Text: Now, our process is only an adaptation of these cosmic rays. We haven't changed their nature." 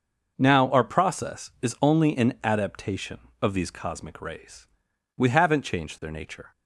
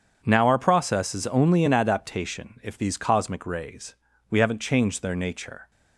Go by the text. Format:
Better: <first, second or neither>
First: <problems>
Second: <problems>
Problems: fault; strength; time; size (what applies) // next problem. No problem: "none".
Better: first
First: none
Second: starts louder than the rest; strong; until 1.2 s; 7.5 dB // says "if" for "of"; at 2.6 s